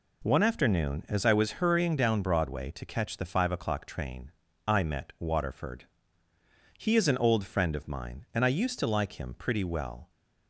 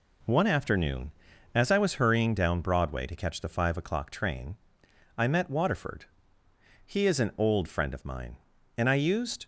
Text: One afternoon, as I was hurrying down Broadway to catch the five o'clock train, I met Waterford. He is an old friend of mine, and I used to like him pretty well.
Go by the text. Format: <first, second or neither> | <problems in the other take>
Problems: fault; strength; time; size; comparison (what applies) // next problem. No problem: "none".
first | stops before "to like him pretty well"; at 9.4 s